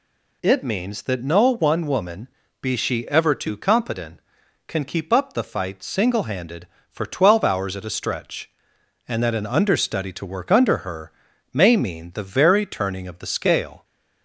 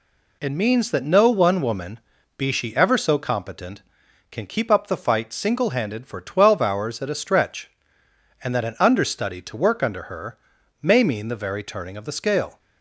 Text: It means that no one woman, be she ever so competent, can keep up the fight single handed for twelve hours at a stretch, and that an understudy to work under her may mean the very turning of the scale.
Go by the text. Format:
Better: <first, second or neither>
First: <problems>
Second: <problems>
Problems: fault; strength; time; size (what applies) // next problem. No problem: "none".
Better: second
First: says "too" for "so"; at 3.3 s // pauses between "her" and "may"; at 11.1 s; 0.40 s long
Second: pauses between "her" and "may"; at 10.3 s; 0.44 s long